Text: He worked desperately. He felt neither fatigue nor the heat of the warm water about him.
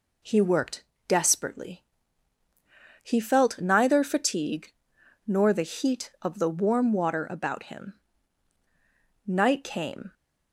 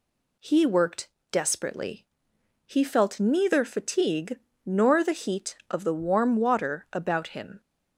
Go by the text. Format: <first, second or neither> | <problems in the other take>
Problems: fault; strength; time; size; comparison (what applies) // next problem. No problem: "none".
second | pauses between "worked" and "desperately"; slight; at 0.8 s; 0.26 s long; slight in the second // pauses between "fatigue" and "nor"; noticeable; at 4.7 s; 0.56 s long; slight in the second // goes on to say "Night came"; noticeable; from 9.2 s on; 0.86 s long